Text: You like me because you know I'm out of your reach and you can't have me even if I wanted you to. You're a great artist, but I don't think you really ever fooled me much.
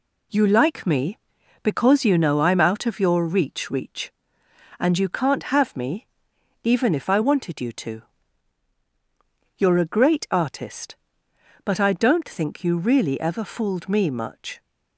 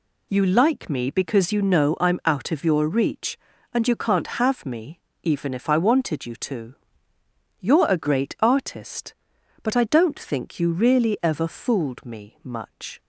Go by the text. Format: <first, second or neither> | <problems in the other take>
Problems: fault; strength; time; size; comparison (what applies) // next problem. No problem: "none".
second | says "reach" twice; at 3.7 s // pauses between "me" and "even"; noticeable; at 6.0 s; 0.56 s long; slight in the second